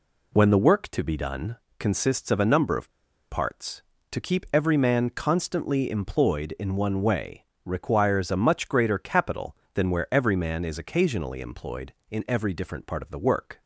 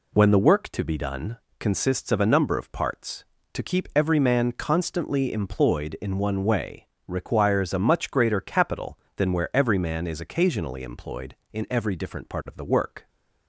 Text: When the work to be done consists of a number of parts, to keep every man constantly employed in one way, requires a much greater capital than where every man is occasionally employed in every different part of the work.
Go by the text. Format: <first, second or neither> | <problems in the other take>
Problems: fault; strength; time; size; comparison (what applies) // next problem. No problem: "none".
second | pauses between "done" and "consists"; slight; at 1.5 s; 0.20 s long; slight in the second // pauses between "of" and "parts"; at 2.9 s; 0.38 s long